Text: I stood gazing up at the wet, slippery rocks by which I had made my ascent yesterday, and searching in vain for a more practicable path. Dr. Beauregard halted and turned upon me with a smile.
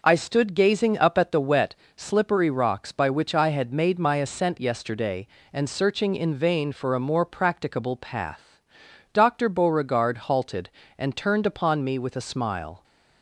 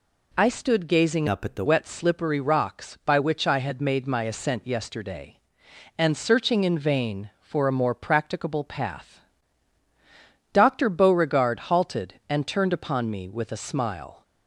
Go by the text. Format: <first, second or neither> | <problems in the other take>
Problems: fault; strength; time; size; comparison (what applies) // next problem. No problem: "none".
first | changes voice from "up" to "the"; from 1.2 to 1.6 s; 0.4 s long